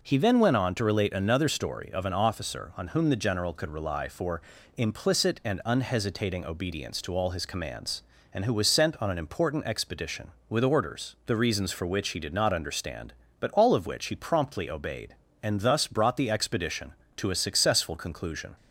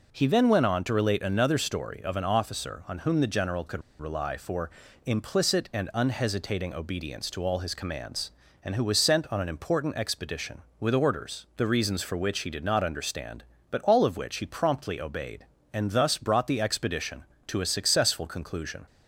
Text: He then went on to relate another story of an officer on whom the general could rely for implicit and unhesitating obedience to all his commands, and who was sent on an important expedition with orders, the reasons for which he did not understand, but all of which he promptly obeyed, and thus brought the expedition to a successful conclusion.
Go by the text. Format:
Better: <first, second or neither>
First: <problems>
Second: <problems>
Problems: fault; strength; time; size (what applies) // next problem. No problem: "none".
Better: first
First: pauses between "for" and "implicit"; slight; at 4.4 s; 0.36 s long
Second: pauses between "could" and "rely"; slight; at 3.8 s; 0.18 s long // pauses between "for" and "implicit"; slight; at 4.6 s; 0.36 s long